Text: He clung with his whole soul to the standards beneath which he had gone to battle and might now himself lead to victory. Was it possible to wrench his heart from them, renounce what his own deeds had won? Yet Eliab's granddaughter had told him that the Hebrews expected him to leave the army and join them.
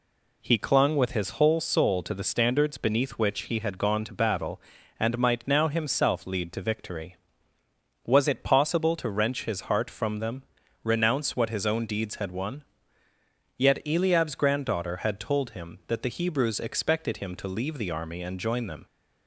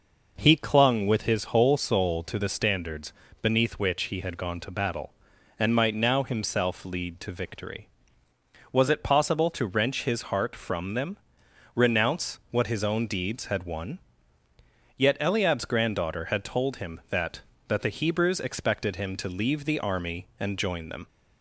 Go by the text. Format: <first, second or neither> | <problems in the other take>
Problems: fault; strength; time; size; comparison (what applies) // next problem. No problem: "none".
first | pauses between "standards" and "beneath"; slight; at 3.1 s; 0.28 s long // says "that" twice; at 17.6 s